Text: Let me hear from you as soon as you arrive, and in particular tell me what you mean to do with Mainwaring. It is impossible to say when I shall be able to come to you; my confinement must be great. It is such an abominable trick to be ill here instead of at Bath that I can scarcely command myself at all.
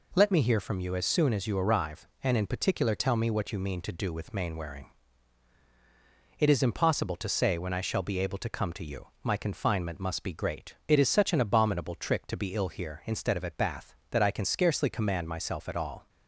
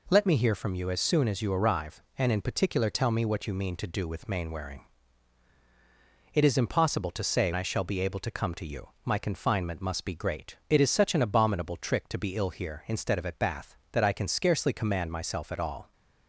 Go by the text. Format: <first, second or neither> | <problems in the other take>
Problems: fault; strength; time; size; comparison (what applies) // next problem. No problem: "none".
first | skips "when"; at 7.5 s